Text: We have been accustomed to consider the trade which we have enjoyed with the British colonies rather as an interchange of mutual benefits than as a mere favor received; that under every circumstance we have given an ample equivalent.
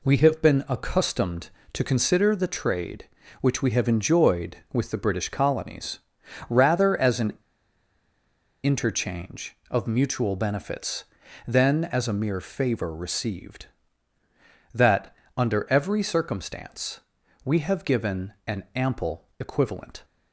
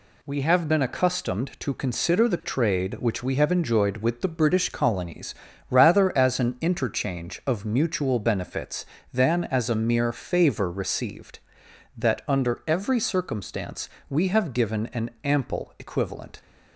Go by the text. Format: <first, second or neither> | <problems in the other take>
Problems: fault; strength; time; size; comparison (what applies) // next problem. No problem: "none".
second | pauses between "colonies" and "rather"; noticeable; at 5.9 s; 0.50 s long; slight in the second // pauses between "an" and "interchange"; strong; at 7.3 s; 1.3 s long // pauses between "that" and "under"; slight; at 15.1 s; 0.20 s long // pauses between "circumstance" and "we"; at 17.0 s; 0.42 s long; slight in the second